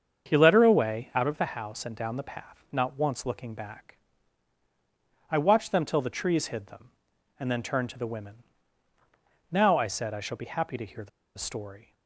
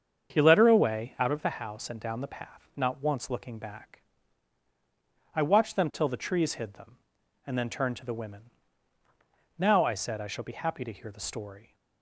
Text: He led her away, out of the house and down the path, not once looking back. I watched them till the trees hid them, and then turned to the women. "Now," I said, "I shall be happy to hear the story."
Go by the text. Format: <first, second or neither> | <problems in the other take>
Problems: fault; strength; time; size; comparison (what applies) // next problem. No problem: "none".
second | starts louder than the rest; strong; until 1.3 s; 7 dB; strong in the second // pauses between "the" and "story"; slight; at 11.0 s; 0.28 s long